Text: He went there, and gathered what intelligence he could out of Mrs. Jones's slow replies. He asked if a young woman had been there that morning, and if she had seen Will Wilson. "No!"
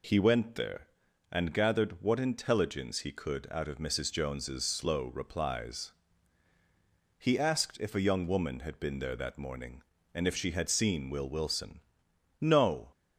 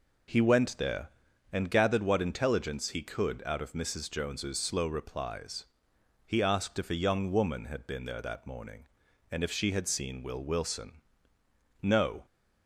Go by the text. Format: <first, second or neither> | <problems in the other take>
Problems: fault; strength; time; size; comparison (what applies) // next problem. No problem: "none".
neither | none